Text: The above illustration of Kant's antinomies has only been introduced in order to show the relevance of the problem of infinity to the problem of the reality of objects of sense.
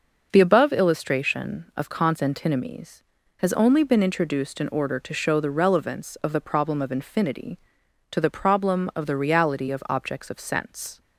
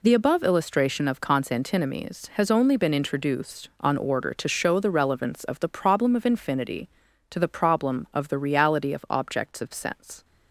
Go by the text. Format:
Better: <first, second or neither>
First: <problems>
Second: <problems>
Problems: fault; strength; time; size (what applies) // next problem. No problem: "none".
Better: first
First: none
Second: says "on" for "in"; at 3.8 s